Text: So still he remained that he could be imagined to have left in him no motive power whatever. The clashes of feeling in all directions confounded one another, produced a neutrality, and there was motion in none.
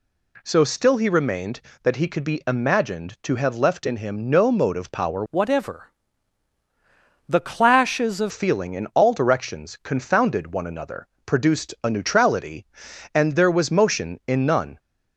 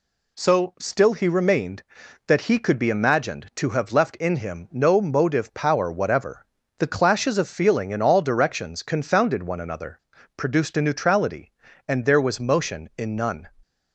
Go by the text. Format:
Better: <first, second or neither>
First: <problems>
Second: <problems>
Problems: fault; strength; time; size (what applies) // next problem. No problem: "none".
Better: second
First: changes voice from "whatever" to "of"; from 5.3 to 8.3 s; 3.0 s long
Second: none